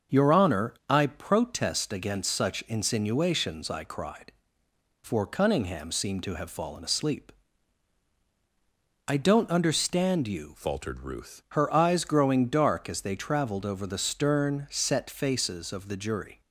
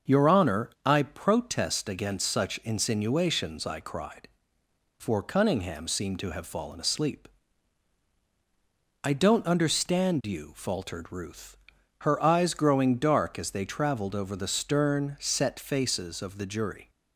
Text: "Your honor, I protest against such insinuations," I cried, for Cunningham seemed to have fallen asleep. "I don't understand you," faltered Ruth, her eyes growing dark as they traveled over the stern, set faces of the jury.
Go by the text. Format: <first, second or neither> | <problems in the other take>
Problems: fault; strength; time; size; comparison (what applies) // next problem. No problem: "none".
second | starts louder than the rest; until 1.2 s; 6.5 dB; also in the second // changes voice from "faltered" to "Ruth"; from 10.5 to 11.4 s; 0.9 s long